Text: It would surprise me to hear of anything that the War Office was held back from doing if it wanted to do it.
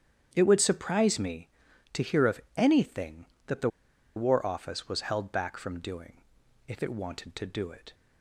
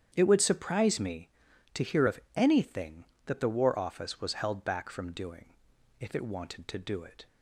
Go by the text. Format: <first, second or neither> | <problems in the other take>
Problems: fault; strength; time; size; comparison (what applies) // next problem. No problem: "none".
second | starts louder than the rest; strong; until 1.3 s; 9 dB; strong in the second // pauses between "of" and "anything"; slight; at 2.4 s; 0.16 s long; slight in the second // pauses between "the" and "War"; noticeable; at 3.6 s; 0.47 s long // pauses between "doing" and "if"; noticeable; at 6.1 s; 0.48 s long; noticeable in the second